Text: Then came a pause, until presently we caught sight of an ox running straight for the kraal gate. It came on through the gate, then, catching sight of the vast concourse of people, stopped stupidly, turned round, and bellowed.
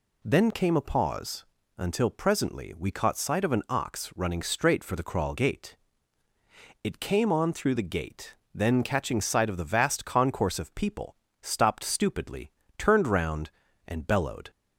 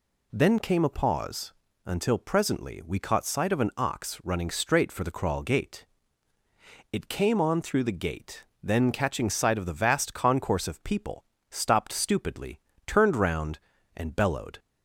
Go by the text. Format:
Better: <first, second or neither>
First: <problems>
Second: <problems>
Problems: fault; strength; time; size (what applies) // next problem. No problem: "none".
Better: neither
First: none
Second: none